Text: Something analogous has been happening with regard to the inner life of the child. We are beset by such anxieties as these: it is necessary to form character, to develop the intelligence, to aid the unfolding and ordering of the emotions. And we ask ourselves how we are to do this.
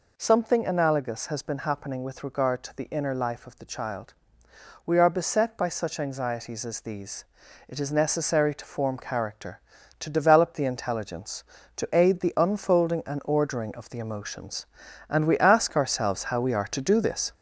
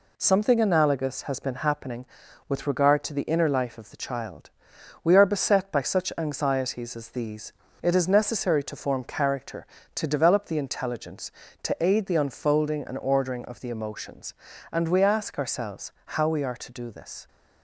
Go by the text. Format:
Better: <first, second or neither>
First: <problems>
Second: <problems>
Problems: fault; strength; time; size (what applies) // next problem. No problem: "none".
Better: second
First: gets louder; noticeable; throughout; 5 dB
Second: none